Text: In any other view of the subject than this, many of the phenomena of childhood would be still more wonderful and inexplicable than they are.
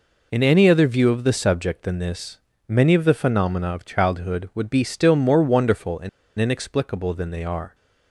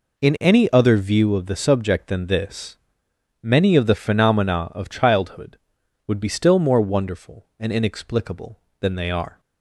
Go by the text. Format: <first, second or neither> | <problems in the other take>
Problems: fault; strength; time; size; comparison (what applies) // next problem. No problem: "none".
second | pauses between "and" and "inexplicable"; slight; at 6.0 s; 0.29 s long